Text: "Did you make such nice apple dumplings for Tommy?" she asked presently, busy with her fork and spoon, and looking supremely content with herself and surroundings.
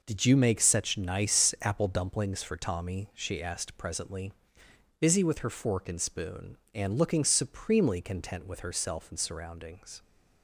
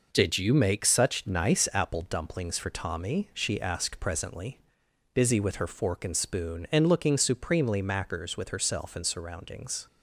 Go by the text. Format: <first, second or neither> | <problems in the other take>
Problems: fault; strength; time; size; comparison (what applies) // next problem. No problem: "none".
first | says "mackers" for "content"; at 7.8 s